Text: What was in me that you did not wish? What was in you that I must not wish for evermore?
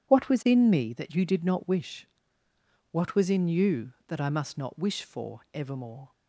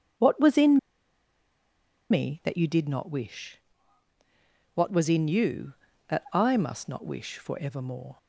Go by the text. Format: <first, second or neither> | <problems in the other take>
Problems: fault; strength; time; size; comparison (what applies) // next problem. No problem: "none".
first | starts louder than the rest; until 2.5 s; 7 dB // pauses between "in" and "me"; strong; at 0.7 s; 1.3 s long